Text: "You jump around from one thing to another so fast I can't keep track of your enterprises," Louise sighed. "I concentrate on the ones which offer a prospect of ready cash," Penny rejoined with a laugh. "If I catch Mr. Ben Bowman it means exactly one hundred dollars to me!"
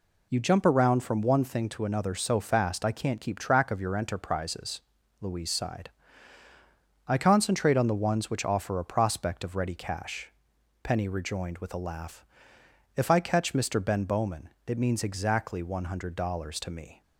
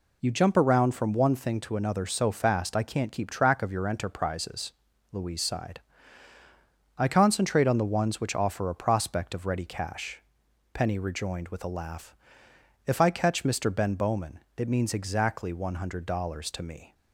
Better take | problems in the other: neither | pauses between "Bowman" and "it"; slight; the same in both

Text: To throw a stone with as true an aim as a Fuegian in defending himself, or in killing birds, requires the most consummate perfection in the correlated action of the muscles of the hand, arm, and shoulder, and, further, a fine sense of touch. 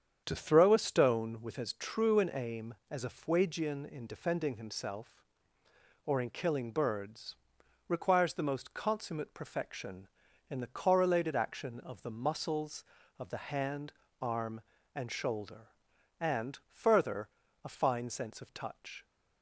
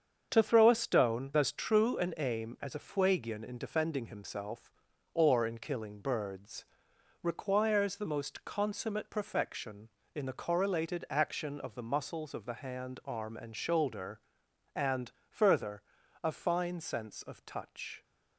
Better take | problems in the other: first | starts louder than the rest; strong; until 1.3 s; 7 dB; strong in the first // skips "with"; at 1.3 s

